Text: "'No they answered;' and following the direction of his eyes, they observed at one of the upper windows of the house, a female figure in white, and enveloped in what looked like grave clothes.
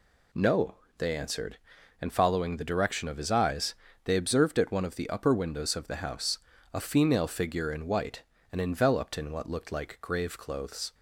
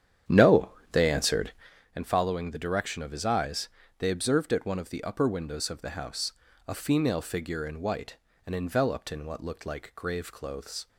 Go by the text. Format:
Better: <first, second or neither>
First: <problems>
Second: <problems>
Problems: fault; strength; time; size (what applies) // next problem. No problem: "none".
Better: first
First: pauses between "No" and "they"; slight; at 0.7 s; 0.22 s long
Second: starts louder than the rest; strong; until 1.7 s; 9.5 dB // pauses between "No" and "they"; slight; at 0.6 s; 0.22 s long